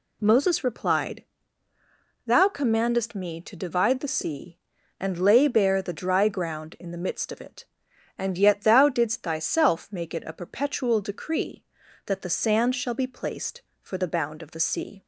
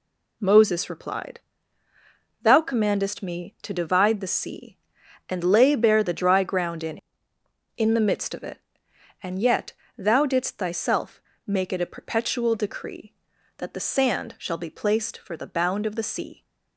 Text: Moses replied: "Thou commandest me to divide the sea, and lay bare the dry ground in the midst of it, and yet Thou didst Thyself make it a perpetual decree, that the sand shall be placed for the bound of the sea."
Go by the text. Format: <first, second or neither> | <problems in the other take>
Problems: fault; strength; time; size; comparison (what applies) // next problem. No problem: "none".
first | says "in" twice; at 7.7 s // pauses between "yet" and "Thou"; slight; at 9.7 s; 0.24 s long // pauses between "Thyself" and "make"; slight; at 11.2 s; 0.24 s long